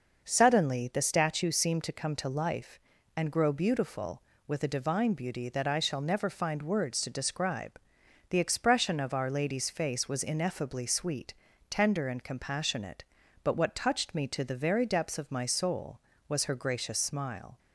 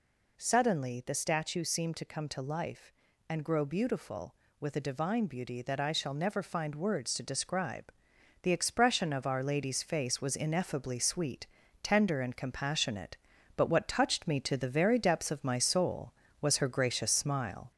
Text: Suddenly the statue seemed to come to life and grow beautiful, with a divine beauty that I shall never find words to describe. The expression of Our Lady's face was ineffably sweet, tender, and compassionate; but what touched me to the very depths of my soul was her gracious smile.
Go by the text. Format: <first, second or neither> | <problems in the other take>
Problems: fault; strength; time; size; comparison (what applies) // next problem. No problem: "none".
first | gets louder; slight; throughout; 2.5 dB